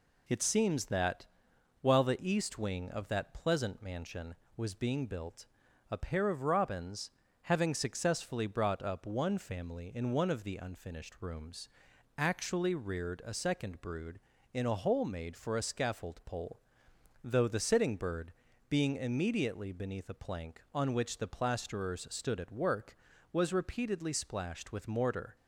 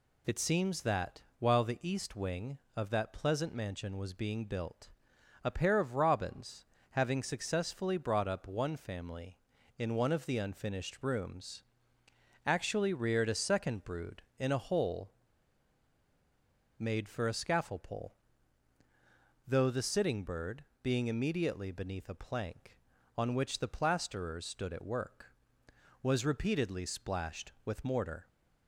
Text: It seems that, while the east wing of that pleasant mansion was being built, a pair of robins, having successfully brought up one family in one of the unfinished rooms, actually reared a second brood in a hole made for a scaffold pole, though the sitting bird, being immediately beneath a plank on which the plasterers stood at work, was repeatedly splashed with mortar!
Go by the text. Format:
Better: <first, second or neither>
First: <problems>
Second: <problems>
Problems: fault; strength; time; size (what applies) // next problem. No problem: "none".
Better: first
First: none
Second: pauses between "hole" and "made"; strong; at 15.1 s; 1.6 s long